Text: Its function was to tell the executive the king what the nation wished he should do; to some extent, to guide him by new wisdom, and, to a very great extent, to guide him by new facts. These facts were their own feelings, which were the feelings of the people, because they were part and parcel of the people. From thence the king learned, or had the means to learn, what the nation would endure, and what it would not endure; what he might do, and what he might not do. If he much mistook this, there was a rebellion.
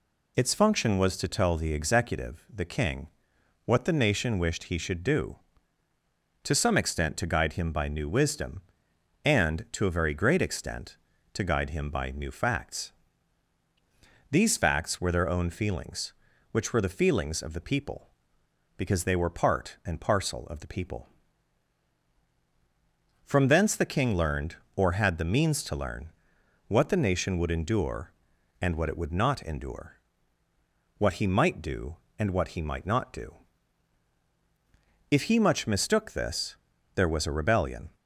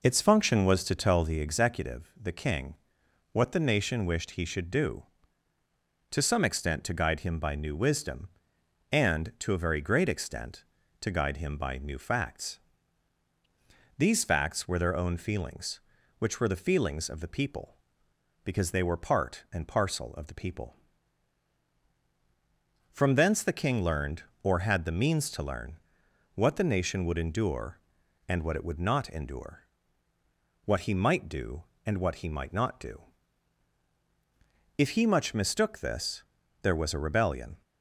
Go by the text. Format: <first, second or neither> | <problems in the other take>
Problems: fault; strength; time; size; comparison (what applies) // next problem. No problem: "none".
first | starts louder than the rest; noticeable; until 1.4 s; 4.5 dB // pauses between "king" and "what"; noticeable; at 2.7 s; 0.58 s long; noticeable in the first